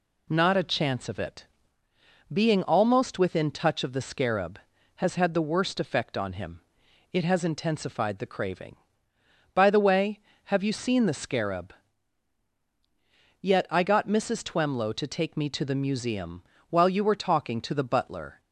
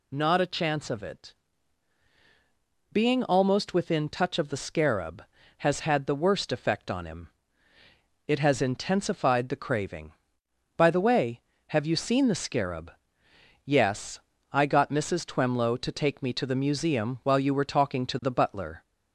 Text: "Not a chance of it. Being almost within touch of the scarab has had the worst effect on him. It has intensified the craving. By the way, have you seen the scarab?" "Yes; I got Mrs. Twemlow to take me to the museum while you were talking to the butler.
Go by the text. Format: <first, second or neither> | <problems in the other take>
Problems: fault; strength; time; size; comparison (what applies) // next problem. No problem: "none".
second | says "Yet" for "Yes"; at 13.3 s // pauses between "museum" and "while"; slight; at 16.4 s; 0.28 s long